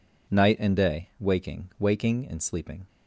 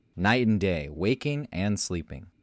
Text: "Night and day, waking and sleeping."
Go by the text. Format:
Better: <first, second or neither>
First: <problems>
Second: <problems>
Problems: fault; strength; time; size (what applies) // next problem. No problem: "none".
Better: second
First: says "waking" twice; at 1.7 s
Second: none